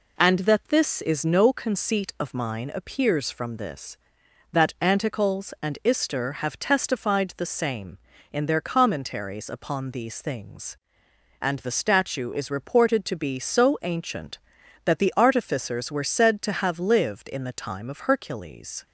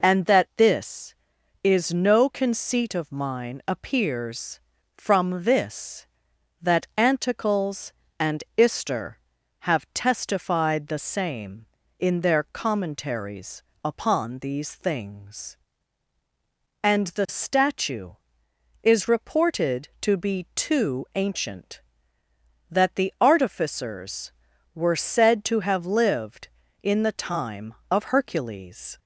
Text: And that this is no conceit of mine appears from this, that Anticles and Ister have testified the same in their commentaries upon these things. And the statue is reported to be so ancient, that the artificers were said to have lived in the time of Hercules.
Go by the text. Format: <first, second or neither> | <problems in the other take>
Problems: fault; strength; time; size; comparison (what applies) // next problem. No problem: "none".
first | pauses between "commentaries" and "upon"; slight; at 13.6 s; 0.22 s long // says "too" for "so"; at 20.5 s